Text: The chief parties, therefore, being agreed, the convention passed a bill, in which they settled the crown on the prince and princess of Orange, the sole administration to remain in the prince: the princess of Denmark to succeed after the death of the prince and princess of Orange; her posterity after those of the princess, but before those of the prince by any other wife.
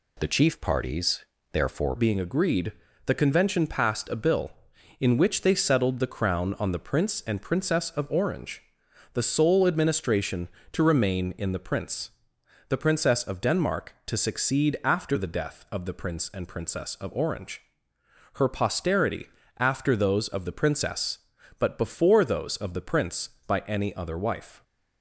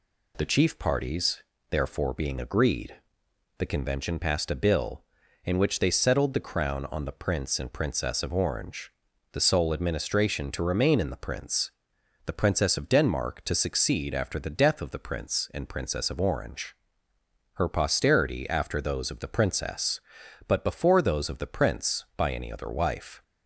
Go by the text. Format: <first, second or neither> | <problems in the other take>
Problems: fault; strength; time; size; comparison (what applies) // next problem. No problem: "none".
second | changes voice at "being"; from 1.9 s on; 22.7 s long // pauses between "posterity" and "after"; slight; at 19.2 s; 0.32 s long